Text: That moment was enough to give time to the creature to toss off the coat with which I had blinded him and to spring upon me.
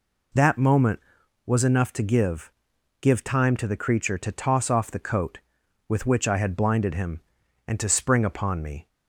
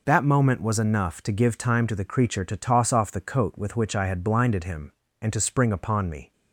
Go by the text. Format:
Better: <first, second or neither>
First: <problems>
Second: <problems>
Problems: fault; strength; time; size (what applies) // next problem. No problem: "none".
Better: second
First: says "give" twice; at 3.0 s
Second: none